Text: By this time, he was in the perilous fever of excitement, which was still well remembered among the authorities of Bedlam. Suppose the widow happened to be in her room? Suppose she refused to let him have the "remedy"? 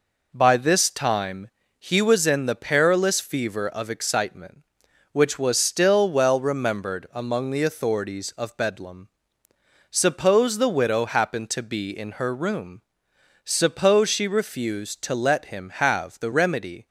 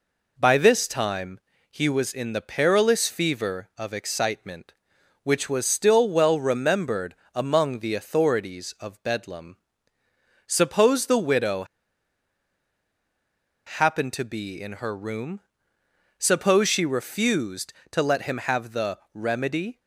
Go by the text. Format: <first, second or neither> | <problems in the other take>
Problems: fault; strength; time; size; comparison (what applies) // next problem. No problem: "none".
first | pauses between "remembered" and "among"; slight; at 7.1 s; 0.20 s long // pauses between "widow" and "happened"; strong; at 11.6 s; 2.0 s long // pauses between "the" and "remedy"; slight; at 18.9 s; 0.16 s long